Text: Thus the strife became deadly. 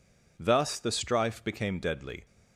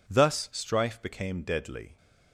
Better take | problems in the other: first | skips "the"; at 0.5 s

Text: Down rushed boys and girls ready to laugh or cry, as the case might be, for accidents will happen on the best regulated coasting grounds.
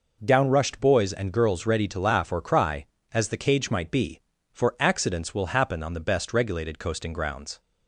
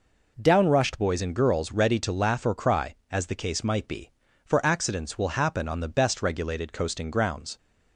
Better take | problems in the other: second | says "cage" for "case"; at 3.3 s

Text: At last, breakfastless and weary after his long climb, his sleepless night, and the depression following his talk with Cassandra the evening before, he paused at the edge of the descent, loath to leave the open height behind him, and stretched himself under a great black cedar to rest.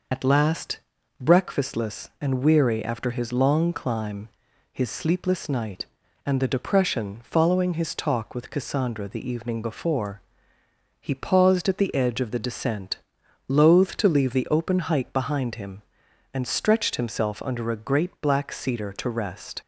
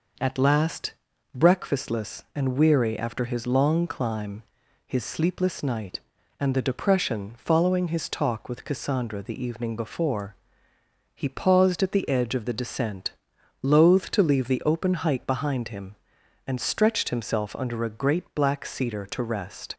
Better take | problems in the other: second | loses the start of "At"; at 0.1 s; 80 ms

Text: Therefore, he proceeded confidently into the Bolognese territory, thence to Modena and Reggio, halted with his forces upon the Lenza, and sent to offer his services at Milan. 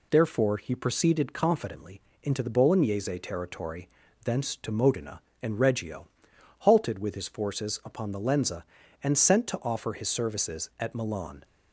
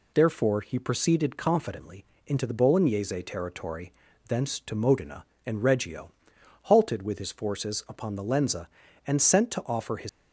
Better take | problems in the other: first | pauses between "confidently" and "into"; slight; at 2.0 s; 0.22 s long; slight in the first // stops before "services at Milan"; at 10.0 s

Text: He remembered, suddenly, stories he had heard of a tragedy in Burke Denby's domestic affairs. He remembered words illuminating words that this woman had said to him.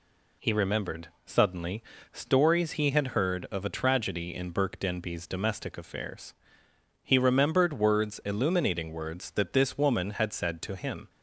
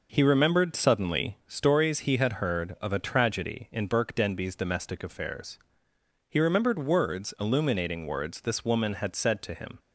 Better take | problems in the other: first | skips "that"; at 8.4 s

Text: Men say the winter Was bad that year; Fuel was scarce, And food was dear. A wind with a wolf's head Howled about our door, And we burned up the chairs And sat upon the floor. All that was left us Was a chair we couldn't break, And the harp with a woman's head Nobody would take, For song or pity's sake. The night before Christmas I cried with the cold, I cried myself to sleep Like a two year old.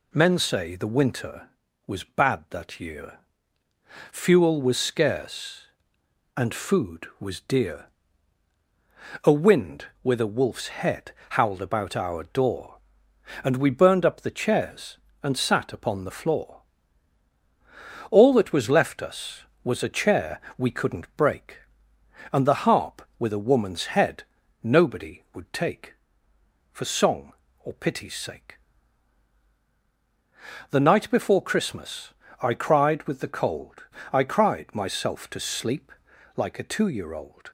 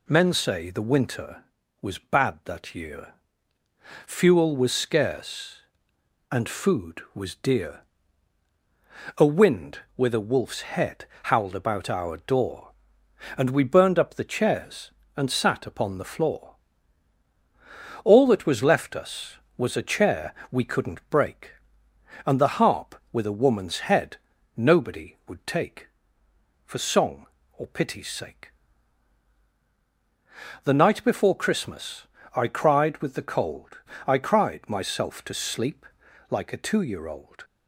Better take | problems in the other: neither | pauses between "head" and "Howled"; slight; the same in both // pauses between "chair" and "we"; slight; the same in both // pauses between "head" and "Nobody"; the same in both // pauses between "Christmas" and "I"; slight; the same in both // pauses between "sleep" and "Like"; the same in both

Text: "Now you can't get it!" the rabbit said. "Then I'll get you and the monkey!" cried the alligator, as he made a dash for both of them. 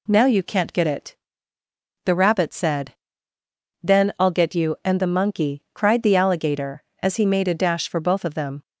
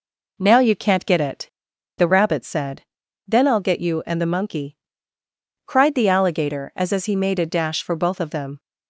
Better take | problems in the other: first | says "as" twice; at 6.9 s

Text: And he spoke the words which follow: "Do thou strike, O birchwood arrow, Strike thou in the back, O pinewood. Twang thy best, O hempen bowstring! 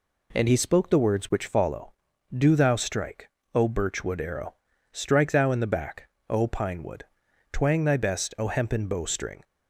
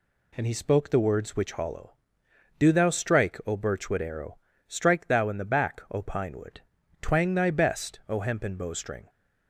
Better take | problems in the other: first | says "hollow" for "follow"; at 1.5 s

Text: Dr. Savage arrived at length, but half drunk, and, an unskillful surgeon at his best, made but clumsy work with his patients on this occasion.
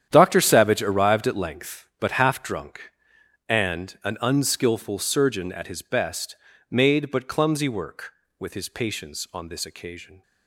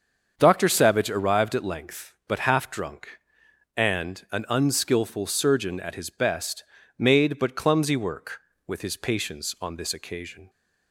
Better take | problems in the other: second | gets quieter; strong; throughout; 13 dB // starts louder than the rest; strong; until 1.1 s; 9.5 dB; also in the second

